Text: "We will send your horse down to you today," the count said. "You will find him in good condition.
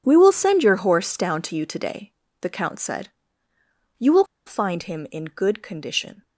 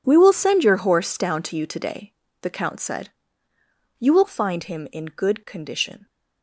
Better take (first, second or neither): second